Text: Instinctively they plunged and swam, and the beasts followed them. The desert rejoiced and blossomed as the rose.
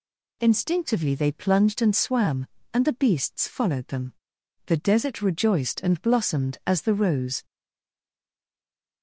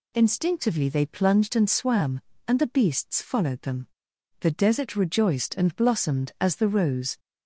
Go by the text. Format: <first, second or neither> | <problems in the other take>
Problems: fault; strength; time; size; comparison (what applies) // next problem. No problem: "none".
second | stays silent after the last word; noticeable; from 7.4 s on; 1.6 s long